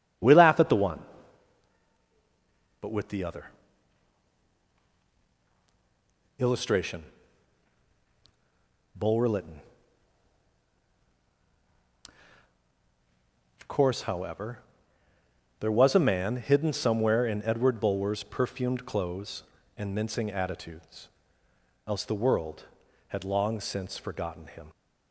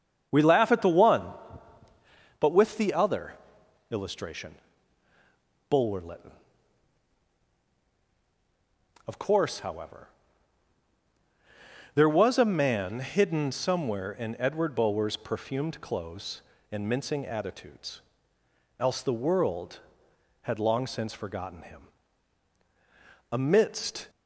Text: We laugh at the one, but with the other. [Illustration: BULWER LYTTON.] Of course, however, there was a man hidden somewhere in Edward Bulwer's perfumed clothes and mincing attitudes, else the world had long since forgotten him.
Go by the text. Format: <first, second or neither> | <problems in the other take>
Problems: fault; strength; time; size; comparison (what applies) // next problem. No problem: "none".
first | starts louder than the rest; strong; until 2.5 s; 7.5 dB; strong in the first // goes on to say "Amidst"; noticeable; from 23.3 s on; 0.78 s long